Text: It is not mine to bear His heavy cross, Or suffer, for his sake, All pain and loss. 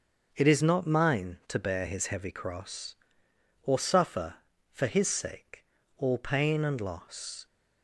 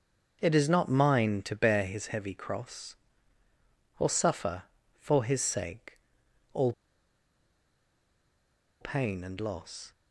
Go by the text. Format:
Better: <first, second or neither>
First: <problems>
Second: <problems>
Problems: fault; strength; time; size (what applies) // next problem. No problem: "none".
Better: first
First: starts louder than the rest; until 1.3 s; 6 dB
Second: starts louder than the rest; until 1.4 s; 6.5 dB // pauses between "All" and "pain"; strong; at 6.7 s; 2.0 s long